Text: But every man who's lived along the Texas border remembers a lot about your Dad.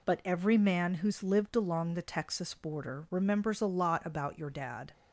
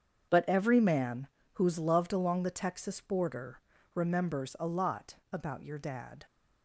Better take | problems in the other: first | starts louder than the rest; strong; until 1.5 s; 7.5 dB // pauses between "man" and "who's"; slight; at 1.2 s; 0.26 s long // says "loved" for "lived"; at 1.7 s // pauses between "border" and "remembers"; slight; at 3.5 s; 0.36 s long // pauses between "lot" and "about"; slight; at 5.1 s; 0.16 s long

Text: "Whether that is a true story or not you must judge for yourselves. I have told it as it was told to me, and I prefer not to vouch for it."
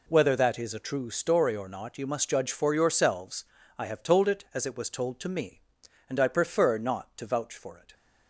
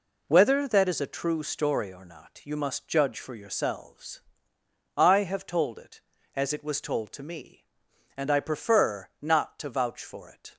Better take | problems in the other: neither | none

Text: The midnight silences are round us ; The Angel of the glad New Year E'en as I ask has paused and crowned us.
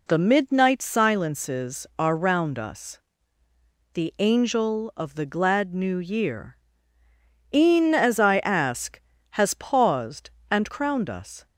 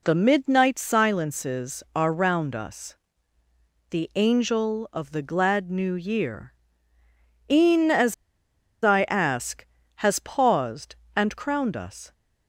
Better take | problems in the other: first | pauses between "Year" and "E'en"; noticeable; at 6.5 s; 0.96 s long; noticeable in the first // pauses between "as" and "I"; noticeable; at 8.1 s; 0.70 s long

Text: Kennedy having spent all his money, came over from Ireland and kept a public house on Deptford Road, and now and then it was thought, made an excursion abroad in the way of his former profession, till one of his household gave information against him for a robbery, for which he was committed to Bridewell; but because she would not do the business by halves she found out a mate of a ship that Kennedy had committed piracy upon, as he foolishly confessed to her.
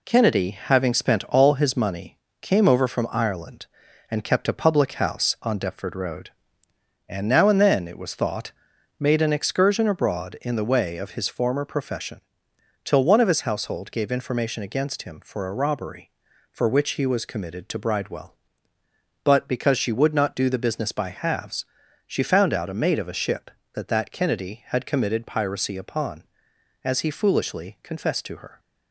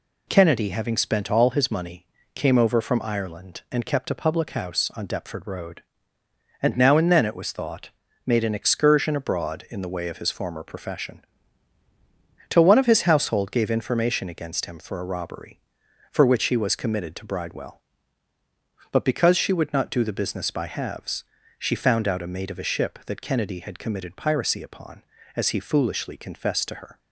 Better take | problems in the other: second | pauses between "halves" and "she"; at 21.6 s; 0.42 s long; slight in the second // says "that" twice; at 23.8 s

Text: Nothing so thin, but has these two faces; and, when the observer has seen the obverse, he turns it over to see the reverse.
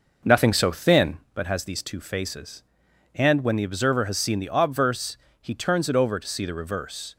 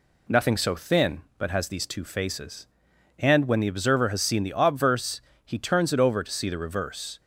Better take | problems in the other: second | starts louder than the rest; noticeable; until 1.4 s; 5.5 dB

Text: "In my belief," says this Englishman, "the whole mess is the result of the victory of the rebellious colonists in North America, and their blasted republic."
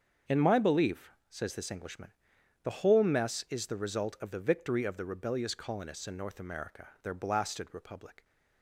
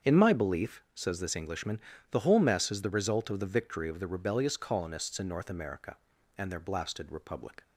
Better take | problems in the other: second | starts louder than the rest; strong; until 1.4 s; 7 dB; strong in the second // skips "and"; at 6.9 s

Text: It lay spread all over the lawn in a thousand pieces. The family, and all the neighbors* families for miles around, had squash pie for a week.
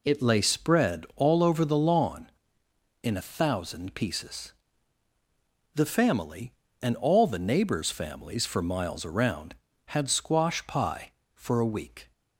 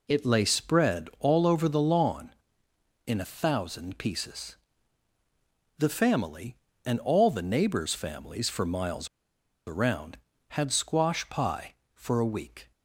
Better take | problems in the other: first | pauses between "miles" and "around"; noticeable; at 9.0 s; 0.59 s long

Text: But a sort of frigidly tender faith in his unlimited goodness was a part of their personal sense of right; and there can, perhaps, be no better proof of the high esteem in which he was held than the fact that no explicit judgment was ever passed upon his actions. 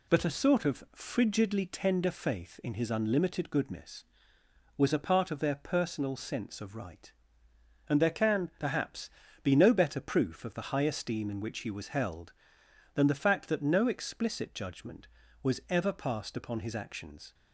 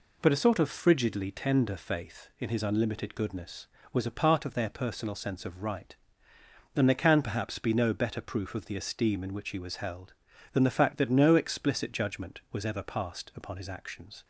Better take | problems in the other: first | skips "high"; at 8.7 s

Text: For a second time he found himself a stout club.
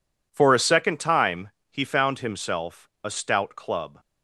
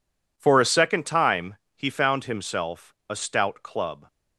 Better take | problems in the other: neither | pauses between "time" and "he"; slight; the same in both // pauses between "himself" and "a"; slight; the same in both

